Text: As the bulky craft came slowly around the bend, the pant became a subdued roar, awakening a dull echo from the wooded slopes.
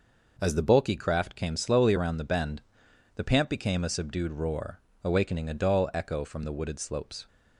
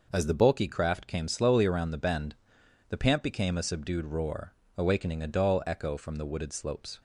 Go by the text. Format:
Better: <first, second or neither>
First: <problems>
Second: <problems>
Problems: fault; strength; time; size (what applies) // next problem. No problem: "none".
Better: neither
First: none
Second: none